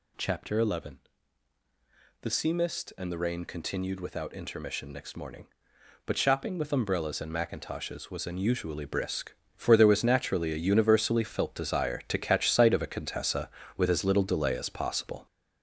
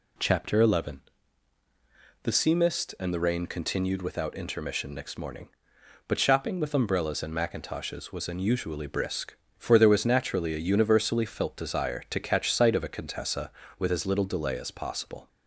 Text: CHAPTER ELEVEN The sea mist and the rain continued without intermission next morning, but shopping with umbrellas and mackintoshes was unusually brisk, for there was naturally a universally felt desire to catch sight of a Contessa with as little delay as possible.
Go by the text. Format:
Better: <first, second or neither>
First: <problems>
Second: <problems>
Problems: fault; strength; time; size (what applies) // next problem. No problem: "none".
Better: second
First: gets louder; noticeable; throughout; 6 dB // pauses between "ELEVEN" and "The"; at 1.0 s; 1.2 s long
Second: pauses between "ELEVEN" and "The"; at 1.0 s; 1.2 s long